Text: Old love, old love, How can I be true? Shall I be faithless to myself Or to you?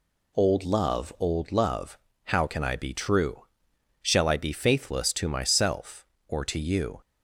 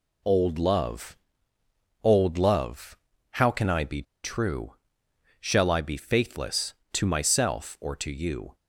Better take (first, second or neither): first